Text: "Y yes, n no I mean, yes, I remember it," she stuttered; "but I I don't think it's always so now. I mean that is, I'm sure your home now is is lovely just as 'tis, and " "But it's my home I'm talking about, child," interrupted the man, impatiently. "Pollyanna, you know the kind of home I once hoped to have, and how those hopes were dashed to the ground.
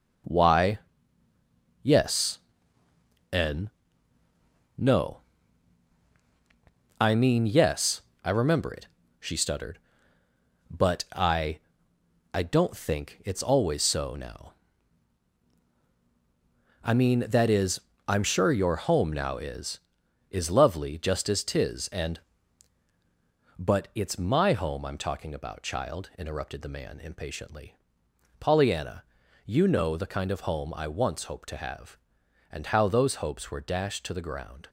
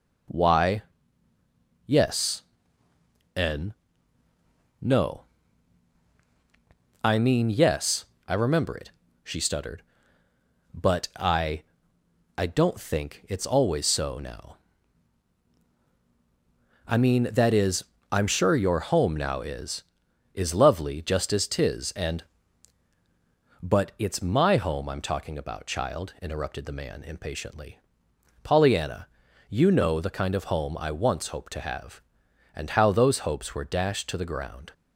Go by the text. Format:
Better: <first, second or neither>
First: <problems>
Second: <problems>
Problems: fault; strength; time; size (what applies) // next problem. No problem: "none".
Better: second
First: gets quieter; strong; throughout; 9 dB // pauses between "Y" and "yes"; at 0.7 s; 1.0 s long // pauses between "n" and "no"; at 3.6 s; 1.0 s long // pauses between "no" and "I"; strong; at 5.2 s; 1.7 s long // pauses between "I" and "I"; noticeable; at 11.5 s; 0.74 s long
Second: pauses between "Y" and "yes"; at 0.8 s; 1.0 s long // pauses between "n" and "no"; at 3.7 s; 1.0 s long // pauses between "no" and "I"; strong; at 5.2 s; 1.7 s long // pauses between "I" and "I"; noticeable; at 11.6 s; 0.74 s long